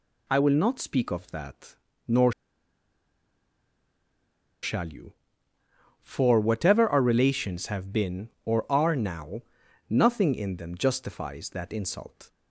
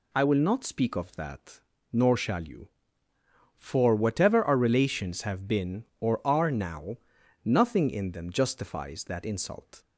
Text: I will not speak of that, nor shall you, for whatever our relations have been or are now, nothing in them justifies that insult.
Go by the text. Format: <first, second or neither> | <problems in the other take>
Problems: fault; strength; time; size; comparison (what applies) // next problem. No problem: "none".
second | pauses between "nor" and "shall"; strong; at 2.3 s; 2.3 s long